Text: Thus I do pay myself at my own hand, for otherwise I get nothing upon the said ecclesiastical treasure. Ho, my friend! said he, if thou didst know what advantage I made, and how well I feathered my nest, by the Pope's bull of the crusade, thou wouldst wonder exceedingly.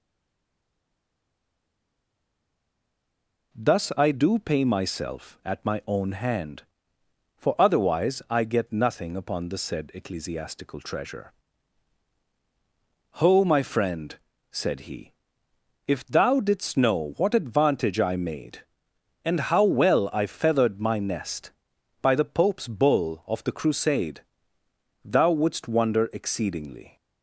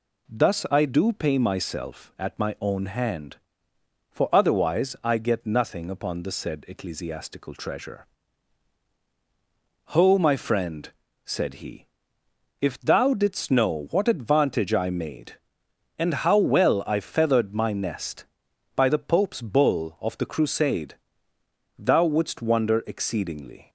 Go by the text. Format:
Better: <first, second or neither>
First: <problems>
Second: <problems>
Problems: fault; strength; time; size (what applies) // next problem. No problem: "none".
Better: second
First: stays silent before the first word; strong; until 3.5 s; 3.5 s long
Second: none